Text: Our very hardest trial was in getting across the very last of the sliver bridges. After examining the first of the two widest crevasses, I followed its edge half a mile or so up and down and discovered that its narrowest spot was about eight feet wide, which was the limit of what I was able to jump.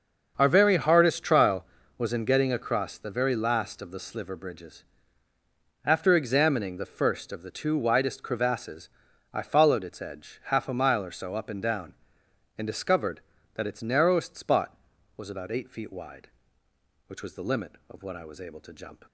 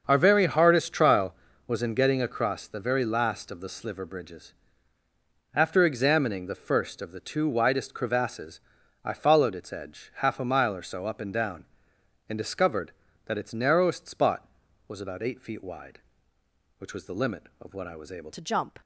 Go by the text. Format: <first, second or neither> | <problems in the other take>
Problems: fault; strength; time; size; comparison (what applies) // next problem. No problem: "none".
first | starts louder than the rest; until 1.0 s; 6.5 dB; also in the first // changes voice at "to"; from 18.3 s on; 0.4 s long